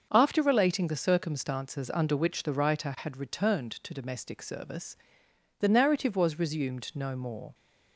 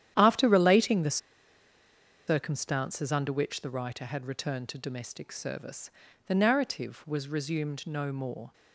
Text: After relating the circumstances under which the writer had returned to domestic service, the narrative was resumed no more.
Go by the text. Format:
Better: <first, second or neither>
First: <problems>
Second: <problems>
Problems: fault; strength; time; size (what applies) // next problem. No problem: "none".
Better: first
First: starts louder than the rest; until 1.1 s; 6.5 dB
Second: starts louder than the rest; strong; until 1.1 s; 10.5 dB // pauses between "the" and "circumstances"; at 1.1 s; 1.1 s long